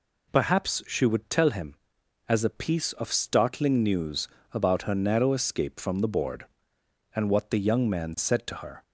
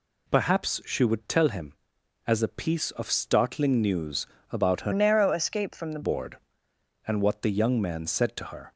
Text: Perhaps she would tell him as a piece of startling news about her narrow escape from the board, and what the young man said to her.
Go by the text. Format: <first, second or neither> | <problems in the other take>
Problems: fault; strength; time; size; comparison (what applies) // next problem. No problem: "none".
first | pauses between "news" and "about"; slight; at 4.2 s; 0.24 s long; slight in the first // changes voice from "narrow" to "the"; from 4.9 to 6.0 s; 1.1 s long